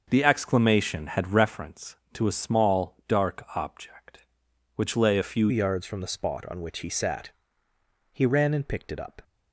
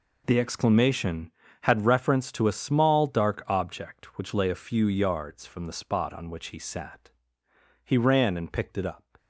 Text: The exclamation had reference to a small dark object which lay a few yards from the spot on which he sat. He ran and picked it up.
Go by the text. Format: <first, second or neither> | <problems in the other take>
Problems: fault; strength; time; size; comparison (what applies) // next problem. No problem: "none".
second | starts louder than the rest; until 1.1 s; 6 dB // changes voice at "yards"; from 5.4 s on; 3.8 s long